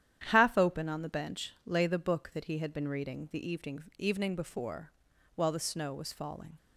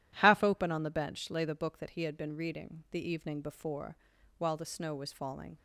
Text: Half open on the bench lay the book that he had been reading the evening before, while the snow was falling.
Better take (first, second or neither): second